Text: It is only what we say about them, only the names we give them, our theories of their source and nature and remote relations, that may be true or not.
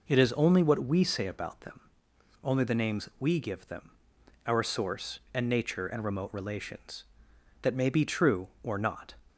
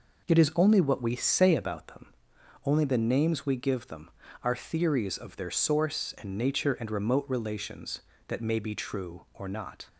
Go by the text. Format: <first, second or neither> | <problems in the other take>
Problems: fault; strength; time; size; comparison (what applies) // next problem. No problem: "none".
second | skips "theories of their"; at 4.6 s